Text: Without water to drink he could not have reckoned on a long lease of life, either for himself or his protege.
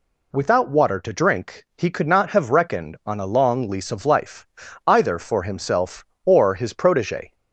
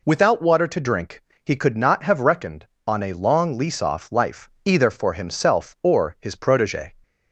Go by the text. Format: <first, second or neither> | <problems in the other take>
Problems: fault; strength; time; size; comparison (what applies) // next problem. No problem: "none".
first | pauses between "drink" and "he"; slight; at 1.2 s; 0.22 s long // says "off" for "of"; at 3.8 s